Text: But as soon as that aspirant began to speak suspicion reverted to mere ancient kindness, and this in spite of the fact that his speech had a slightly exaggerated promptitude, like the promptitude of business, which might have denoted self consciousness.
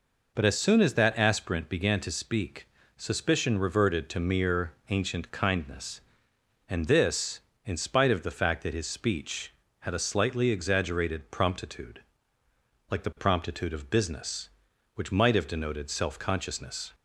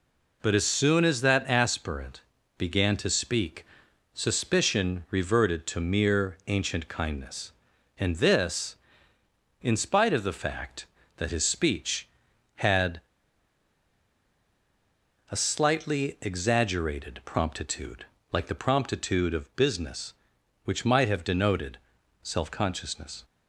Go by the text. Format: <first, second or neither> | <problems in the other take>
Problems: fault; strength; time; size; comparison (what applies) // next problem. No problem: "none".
first | pauses between "aspirant" and "began"; slight; at 2.2 s; 0.36 s long // pauses between "speak" and "suspicion"; noticeable; at 3.6 s; 0.48 s long; slight in the first // pauses between "had" and "a"; strong; at 13.0 s; 2.2 s long // pauses between "denoted" and "self"; noticeable; at 21.7 s; 0.46 s long